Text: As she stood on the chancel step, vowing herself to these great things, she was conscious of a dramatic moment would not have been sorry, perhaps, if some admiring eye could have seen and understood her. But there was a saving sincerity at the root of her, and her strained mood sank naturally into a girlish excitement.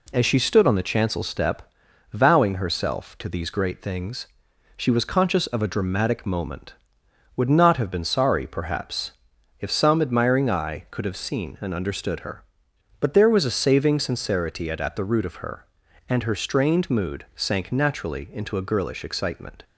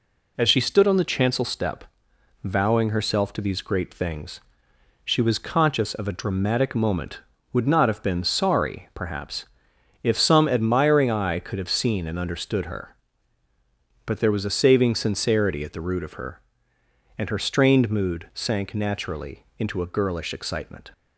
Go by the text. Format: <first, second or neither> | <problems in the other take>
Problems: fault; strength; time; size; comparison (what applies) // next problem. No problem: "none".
second | says "at" twice; at 14.7 s